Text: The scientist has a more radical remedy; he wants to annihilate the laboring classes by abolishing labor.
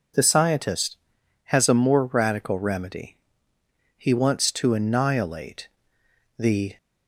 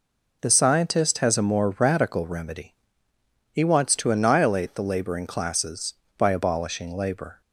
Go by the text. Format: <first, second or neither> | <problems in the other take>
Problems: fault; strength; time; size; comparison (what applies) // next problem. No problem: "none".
second | pauses between "annihilate" and "the"; noticeable; at 5.6 s; 0.68 s long // stops before "laboring classes by abolishing labor"; at 6.7 s